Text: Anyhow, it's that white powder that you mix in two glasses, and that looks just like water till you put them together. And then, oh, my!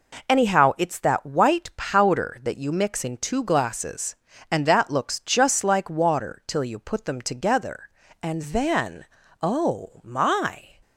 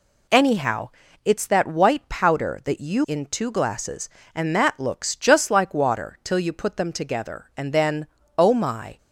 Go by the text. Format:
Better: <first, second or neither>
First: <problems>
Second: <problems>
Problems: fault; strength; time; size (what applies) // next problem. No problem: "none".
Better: first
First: none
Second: skips "mix"; at 3.0 s